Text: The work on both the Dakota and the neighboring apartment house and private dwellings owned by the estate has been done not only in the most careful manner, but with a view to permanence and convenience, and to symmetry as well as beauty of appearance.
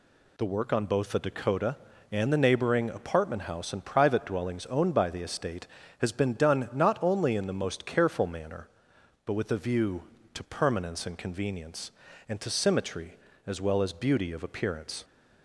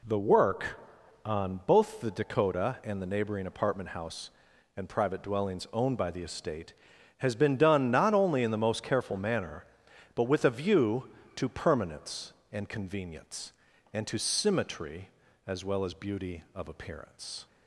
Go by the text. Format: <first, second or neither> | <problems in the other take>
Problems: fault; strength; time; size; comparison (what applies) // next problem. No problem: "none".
neither | none